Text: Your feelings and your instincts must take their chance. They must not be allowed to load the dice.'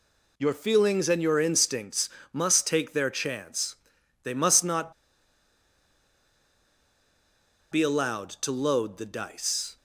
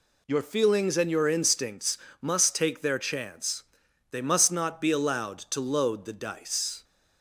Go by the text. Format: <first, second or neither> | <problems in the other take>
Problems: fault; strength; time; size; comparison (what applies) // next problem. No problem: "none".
second | pauses between "instincts" and "must"; slight; at 2.0 s; 0.24 s long; slight in the second // pauses between "not" and "be"; strong; at 4.9 s; 2.8 s long